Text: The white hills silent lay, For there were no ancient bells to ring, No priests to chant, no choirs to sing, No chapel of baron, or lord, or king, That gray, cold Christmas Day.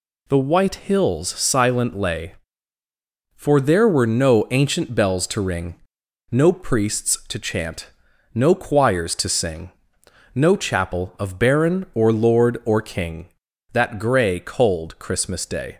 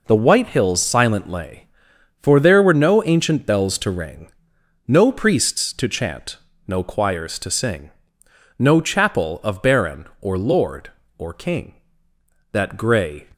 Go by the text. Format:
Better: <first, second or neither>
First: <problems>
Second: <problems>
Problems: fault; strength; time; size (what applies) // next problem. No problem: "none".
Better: first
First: none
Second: stops before "cold Christmas Day"; at 13.3 s